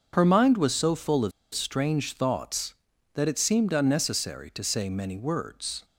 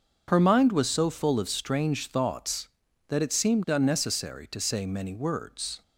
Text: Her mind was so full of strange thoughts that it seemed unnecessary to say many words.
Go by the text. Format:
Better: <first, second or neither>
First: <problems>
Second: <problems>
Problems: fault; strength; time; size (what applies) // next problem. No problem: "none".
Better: second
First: starts louder than the rest; until 1.1 s; 7 dB // pauses between "of" and "strange"; slight; at 1.3 s; 0.23 s long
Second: starts louder than the rest; until 1.2 s; 6.5 dB